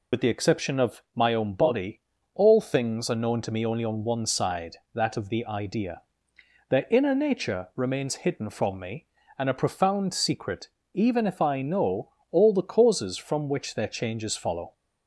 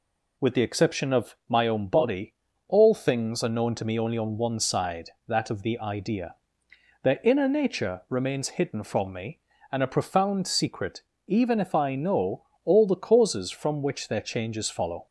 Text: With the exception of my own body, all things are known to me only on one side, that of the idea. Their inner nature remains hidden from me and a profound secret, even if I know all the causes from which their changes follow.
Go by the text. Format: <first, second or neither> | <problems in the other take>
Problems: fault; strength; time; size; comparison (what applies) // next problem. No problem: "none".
second | loses the start of "With"; at 0.1 s; 65 ms // pauses between "know" and "all"; slight; at 12.1 s; 0.20 s long; slight in the second